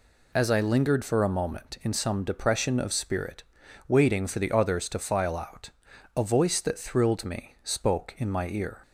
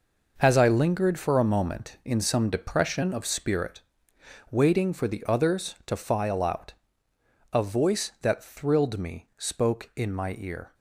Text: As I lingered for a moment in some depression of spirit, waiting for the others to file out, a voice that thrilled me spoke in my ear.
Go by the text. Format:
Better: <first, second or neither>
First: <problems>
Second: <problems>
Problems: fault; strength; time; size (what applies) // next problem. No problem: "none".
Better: first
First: none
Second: gets quieter; strong; throughout; 10 dB